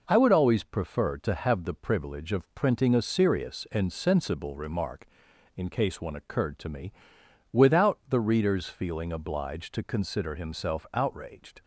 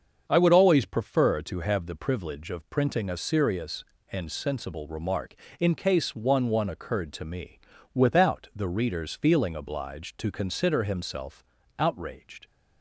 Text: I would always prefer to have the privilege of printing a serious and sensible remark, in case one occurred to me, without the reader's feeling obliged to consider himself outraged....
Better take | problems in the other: first | starts louder than the rest; until 1.3 s; 7 dB // says "one" twice; at 6.4 s // pauses between "himself" and "outraged"; slight; at 11.4 s; 0.34 s long

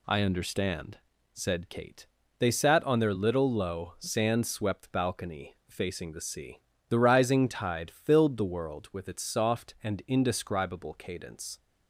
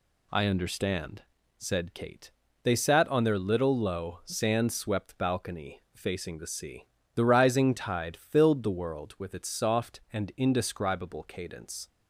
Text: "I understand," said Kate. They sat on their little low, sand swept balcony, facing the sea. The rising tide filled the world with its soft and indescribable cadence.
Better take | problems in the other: neither | none

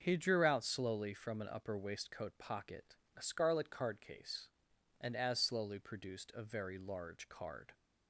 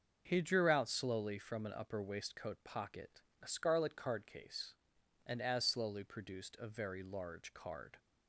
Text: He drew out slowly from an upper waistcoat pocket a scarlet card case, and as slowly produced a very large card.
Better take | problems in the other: neither | starts louder than the rest; the same in both // pauses between "pocket" and "a"; slight; the same in both

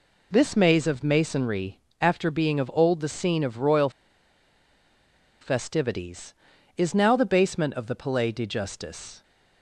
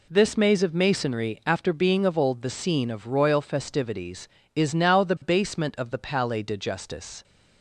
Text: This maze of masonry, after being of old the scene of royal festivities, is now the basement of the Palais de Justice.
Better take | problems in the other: second | pauses between "royal" and "festivities"; strong; at 3.8 s; 1.5 s long

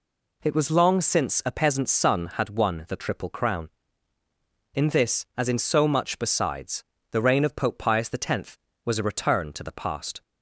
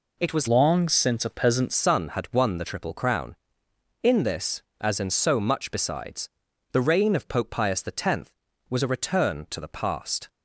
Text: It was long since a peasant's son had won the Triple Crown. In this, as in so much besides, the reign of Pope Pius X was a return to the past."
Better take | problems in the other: first | changes voice from "long" to "peasant's"; from 0.4 to 1.7 s; 1.3 s long

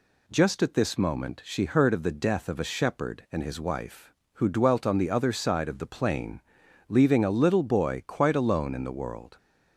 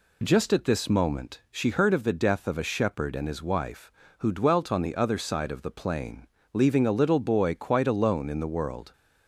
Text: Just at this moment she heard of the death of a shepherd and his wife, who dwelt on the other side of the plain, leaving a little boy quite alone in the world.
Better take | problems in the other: neither | none

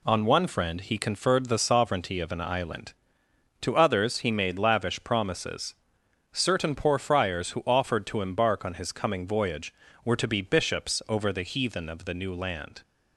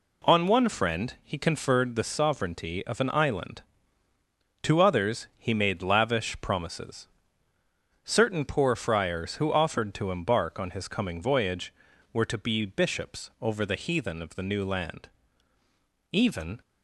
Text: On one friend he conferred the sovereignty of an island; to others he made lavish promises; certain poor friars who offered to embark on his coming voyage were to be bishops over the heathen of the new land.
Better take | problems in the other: first | goes on to say "Even"; slight; from 16.1 s on; 0.48 s long

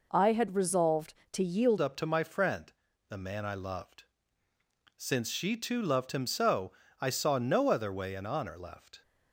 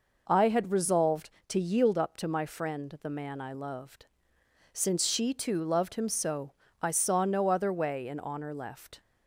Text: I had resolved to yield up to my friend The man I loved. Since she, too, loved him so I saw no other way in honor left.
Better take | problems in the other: second | changes voice at "up"; from 1.7 s on; 7.3 s long // pauses between "friend" and "The"; at 2.6 s; 0.38 s long // pauses between "so" and "I"; slight; at 6.7 s; 0.28 s long; slight in the second

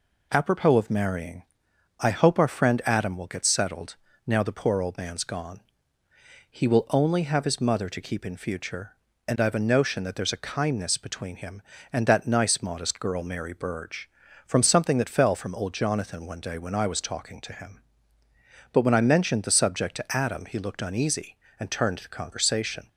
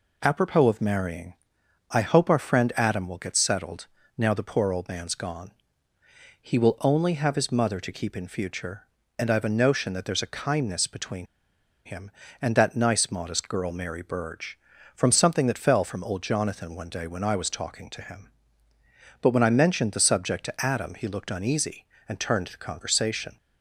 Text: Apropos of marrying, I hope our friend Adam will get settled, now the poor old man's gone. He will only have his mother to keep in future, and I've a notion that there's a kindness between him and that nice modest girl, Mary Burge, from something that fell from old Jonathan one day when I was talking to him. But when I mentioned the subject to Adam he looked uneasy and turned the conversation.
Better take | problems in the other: first | pauses between "between" and "him"; noticeable; at 11.2 s; 0.60 s long

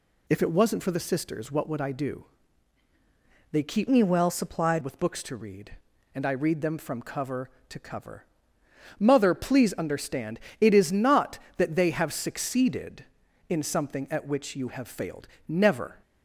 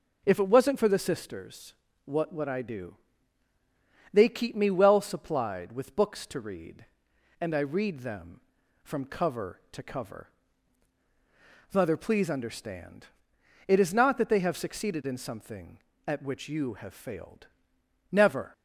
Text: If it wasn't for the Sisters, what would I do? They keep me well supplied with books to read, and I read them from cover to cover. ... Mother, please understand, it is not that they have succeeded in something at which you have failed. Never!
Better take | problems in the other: second | changes voice from "me" to "supplied"; from 3.8 to 4.8 s; 1.0 s long

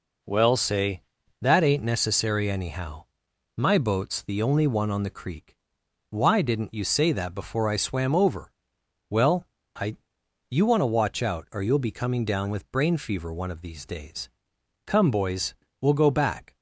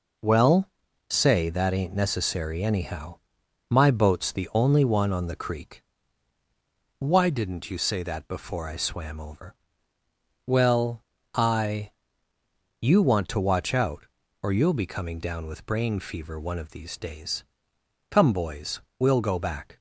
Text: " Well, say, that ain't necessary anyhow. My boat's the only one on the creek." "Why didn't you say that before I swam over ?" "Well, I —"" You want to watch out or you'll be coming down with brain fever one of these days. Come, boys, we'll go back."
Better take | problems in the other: neither | none

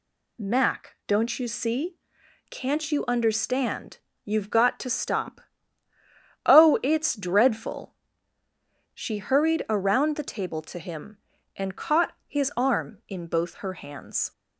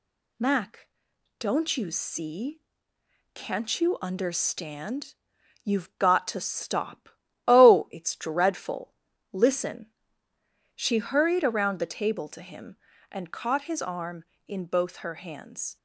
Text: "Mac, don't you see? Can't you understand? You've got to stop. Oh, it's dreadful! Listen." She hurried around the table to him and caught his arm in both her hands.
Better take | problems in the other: second | skips "Listen"; at 8.4 s

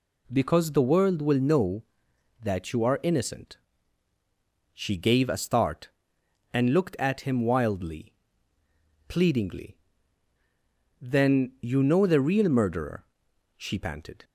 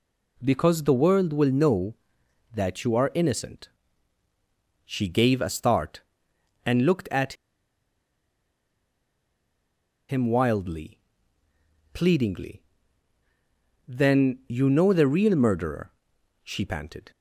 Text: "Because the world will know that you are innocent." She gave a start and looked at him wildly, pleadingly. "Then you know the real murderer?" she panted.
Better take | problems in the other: first | pauses between "at" and "him"; strong; at 7.3 s; 2.7 s long

